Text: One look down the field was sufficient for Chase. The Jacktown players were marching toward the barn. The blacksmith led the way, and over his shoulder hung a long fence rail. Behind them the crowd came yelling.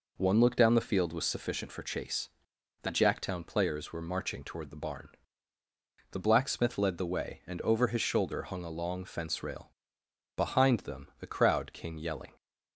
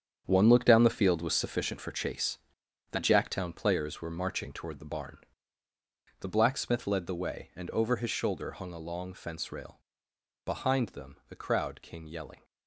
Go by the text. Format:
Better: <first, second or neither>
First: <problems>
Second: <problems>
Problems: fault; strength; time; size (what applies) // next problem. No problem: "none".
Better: first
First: none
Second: gets quieter; strong; throughout; 11 dB